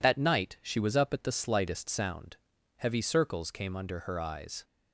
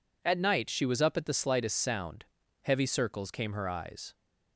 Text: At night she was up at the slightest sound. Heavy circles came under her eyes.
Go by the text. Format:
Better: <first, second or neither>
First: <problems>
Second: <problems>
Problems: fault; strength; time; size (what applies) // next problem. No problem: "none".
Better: first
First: none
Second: skips "under"; at 3.5 s